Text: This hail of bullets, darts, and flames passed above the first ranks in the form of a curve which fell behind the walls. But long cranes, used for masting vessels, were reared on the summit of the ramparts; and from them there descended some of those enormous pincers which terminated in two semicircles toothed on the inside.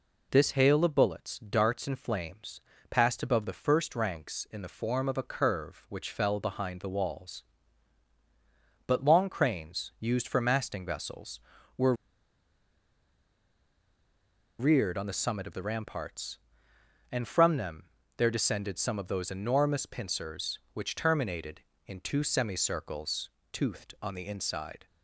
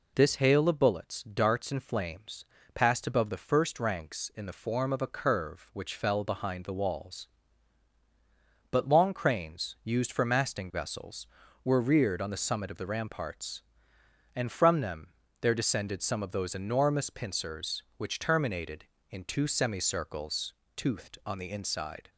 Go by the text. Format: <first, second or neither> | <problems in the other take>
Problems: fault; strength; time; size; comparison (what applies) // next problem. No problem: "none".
second | pauses between "flames" and "passed"; slight; at 2.5 s; 0.30 s long; slight in the second // pauses between "were" and "reared"; strong; at 11.9 s; 2.6 s long // pauses between "them" and "there"; slight; at 17.8 s; 0.32 s long; slight in the second // pauses between "semicircles" and "toothed"; slight; at 23.3 s; 0.22 s long; slight in the second